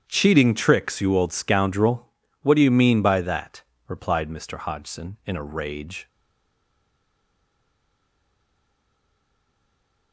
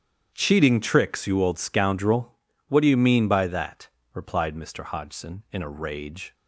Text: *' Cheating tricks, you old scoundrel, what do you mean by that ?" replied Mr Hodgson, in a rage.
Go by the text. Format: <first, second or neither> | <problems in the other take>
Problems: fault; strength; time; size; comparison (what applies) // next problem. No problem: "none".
second | starts louder than the rest; strong; until 1.0 s; 9 dB; strong in the second // stays silent after the last word; strong; from 6.0 s on; 4.1 s long